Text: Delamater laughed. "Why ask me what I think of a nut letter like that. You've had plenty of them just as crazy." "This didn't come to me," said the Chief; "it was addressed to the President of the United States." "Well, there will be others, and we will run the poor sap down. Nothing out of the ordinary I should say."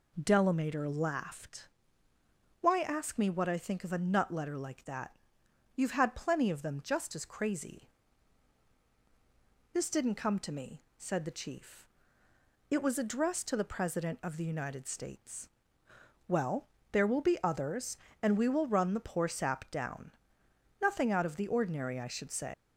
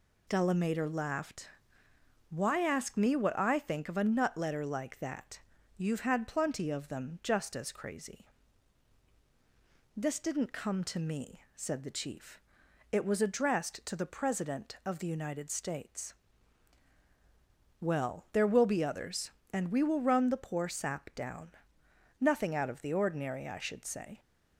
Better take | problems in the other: second | leaves "say" unfinished; at 22.5 s; 140 ms

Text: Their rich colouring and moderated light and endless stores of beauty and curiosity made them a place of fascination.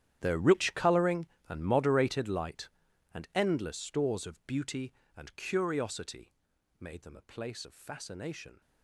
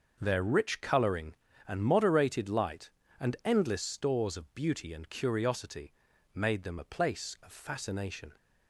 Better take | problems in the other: second | gets quieter; strong; throughout; 18 dB // starts louder than the rest; strong; until 1.2 s; 10.5 dB; noticeable in the second // pauses between "curiosity" and "made"; noticeable; at 6.3 s; 0.46 s long; also in the second

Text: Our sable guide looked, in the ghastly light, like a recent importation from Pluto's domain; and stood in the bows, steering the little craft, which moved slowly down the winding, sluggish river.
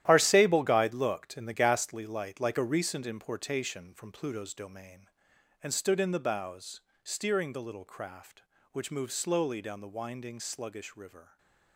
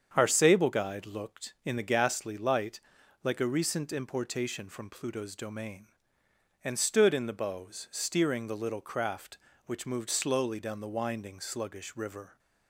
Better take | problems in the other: second | gets quieter; strong; throughout; 11 dB // starts louder than the rest; strong; until 1.0 s; 12.5 dB; strong in the second // stays silent after the last word; slight; from 11.2 s on; 0.5 s long

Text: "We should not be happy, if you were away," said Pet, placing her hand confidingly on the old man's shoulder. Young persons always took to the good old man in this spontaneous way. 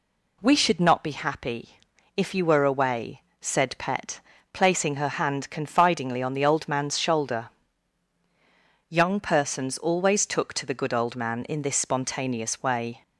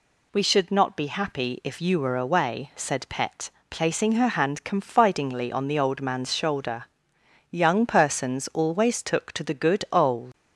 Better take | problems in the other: first | stops before "man in this spontaneous way"; at 10.3 s

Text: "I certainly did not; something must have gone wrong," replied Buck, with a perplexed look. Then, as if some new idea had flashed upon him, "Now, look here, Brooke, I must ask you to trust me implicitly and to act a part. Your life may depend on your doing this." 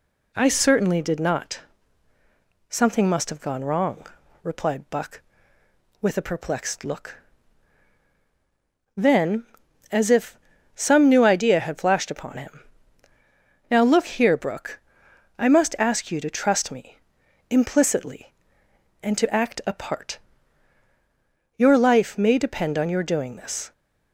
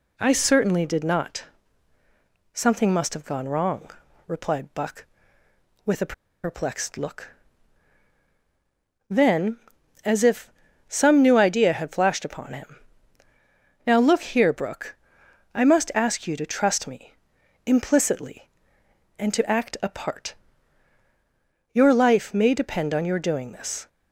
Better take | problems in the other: first | pauses between "a" and "perplexed"; slight; at 6.1 s; 0.30 s long // pauses between "if" and "some"; slight; at 10.5 s; 0.34 s long; slight in the first // pauses between "me" and "implicitly"; noticeable; at 17.1 s; 0.50 s long; noticeable in the first

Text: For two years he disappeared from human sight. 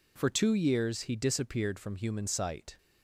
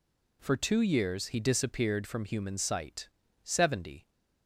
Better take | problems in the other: first | goes on to say "Seventy"; noticeable; from 3.4 s on; 0.66 s long

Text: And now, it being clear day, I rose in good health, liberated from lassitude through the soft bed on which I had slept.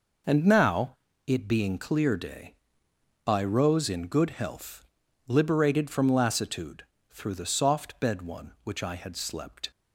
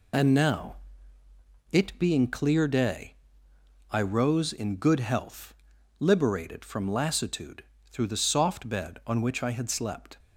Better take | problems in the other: second | pauses between "lassitude" and "through"; slight; at 6.8 s; 0.28 s long; slight in the second // says "one" for "on"; at 8.2 s

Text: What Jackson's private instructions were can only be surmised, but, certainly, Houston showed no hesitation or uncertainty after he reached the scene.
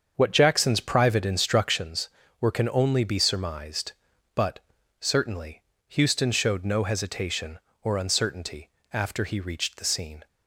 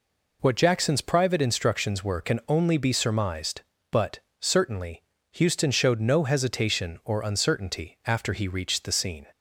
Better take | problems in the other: second | starts louder than the rest; until 1.9 s; 7 dB // pauses between "uncertainty" and "after"; slight; at 8.6 s; 0.24 s long

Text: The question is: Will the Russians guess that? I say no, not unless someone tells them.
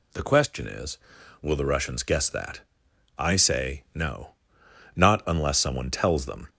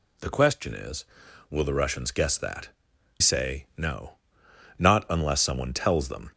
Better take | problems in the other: first | skips "I"; at 2.9 s

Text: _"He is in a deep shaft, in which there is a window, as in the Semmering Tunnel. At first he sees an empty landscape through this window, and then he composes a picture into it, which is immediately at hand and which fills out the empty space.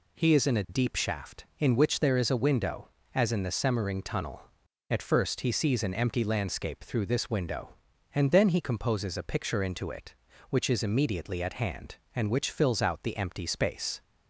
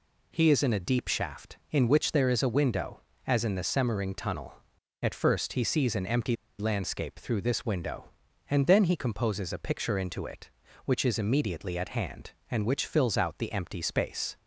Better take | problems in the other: first | pauses between "empty" and "landscape"; slight; at 6.3 s; 0.25 s long

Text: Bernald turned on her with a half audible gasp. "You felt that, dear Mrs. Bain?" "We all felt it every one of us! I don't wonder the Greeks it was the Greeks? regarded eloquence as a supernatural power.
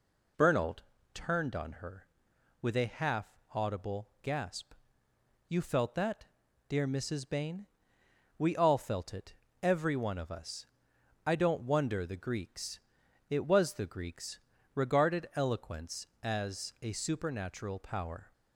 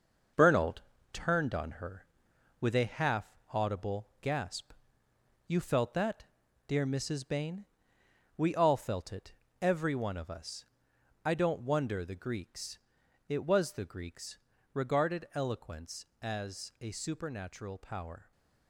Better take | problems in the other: first | gets quieter; throughout; 7 dB // pauses between "Bernald" and "turned"; slight; at 0.8 s; 0.30 s long; slight in the first // pauses between "half" and "audible"; slight; at 3.3 s; 0.16 s long; slight in the first // pauses between "it" and "every"; slight; at 9.3 s; 0.28 s long; slight in the first // pauses between "Greeks" and "it"; noticeable; at 12.7 s; 0.48 s long; noticeable in the first

